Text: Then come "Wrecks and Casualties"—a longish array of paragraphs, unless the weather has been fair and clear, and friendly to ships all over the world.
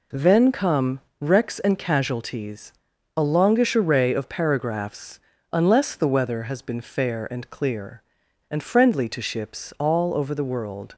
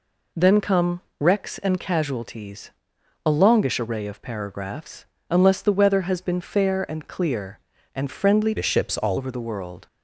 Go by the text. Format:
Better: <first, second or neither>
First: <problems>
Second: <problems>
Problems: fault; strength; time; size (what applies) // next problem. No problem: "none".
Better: first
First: pauses between "come" and "Wrecks"; slight; at 0.9 s; 0.22 s long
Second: pauses between "come" and "Wrecks"; slight; at 1.0 s; 0.18 s long // changes voice from "to" to "all"; from 8.5 to 9.1 s; 0.6 s long